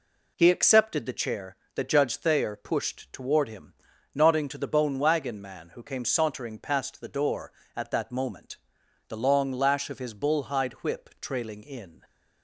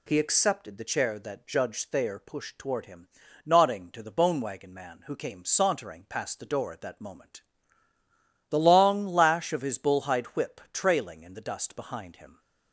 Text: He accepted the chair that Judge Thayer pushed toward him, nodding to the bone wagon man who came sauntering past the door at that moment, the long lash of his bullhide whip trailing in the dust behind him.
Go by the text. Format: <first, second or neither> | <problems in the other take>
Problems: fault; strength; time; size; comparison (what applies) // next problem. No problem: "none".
second | stops before "the dust behind him"; at 12.0 s